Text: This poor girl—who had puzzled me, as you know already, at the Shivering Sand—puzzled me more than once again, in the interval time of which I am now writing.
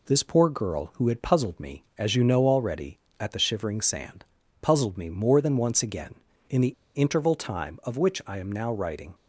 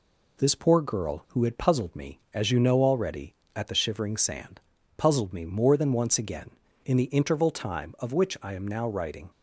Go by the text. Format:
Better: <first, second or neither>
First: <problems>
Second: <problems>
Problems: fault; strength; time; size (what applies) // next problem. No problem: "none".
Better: second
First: pauses between "the" and "interval"; slight; at 6.7 s; 0.20 s long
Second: none